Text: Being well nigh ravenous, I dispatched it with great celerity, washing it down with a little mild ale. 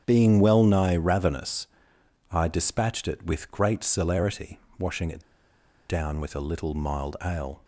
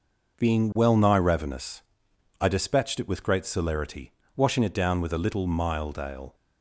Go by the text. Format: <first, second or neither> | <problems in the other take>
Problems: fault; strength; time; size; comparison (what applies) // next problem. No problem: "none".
second | starts louder than the rest; strong; until 1.0 s; 8.5 dB // pauses between "it" and "down"; noticeable; at 5.2 s; 0.66 s long